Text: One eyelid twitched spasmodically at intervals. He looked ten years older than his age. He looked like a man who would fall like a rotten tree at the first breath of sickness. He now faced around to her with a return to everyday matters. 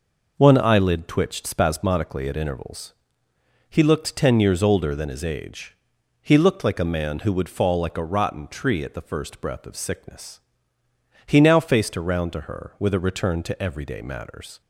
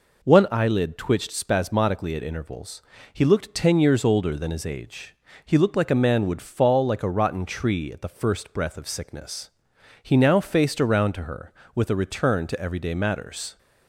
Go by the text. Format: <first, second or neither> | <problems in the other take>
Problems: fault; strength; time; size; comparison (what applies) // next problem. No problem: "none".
first | skips "who"; at 6.2 s